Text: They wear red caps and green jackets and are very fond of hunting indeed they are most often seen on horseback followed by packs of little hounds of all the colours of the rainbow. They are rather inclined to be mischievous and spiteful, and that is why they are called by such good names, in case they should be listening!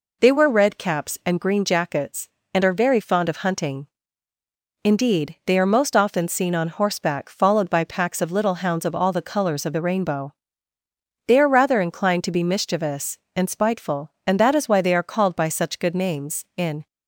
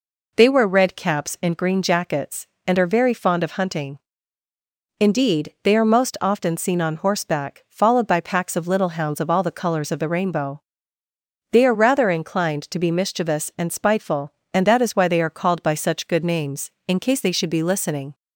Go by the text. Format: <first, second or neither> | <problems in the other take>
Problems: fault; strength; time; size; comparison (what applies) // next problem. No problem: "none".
second | pauses between "hunting" and "indeed"; noticeable; at 3.8 s; 0.96 s long; also in the second // stops before "case they should be listening"; at 16.8 s